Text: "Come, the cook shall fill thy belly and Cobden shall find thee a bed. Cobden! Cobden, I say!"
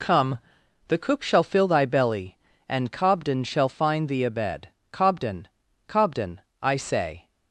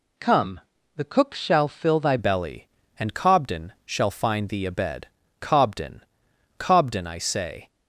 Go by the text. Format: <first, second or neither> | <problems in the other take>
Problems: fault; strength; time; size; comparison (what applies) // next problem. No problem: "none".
first | changes voice at "belly"; from 2.1 s on; 5.5 s long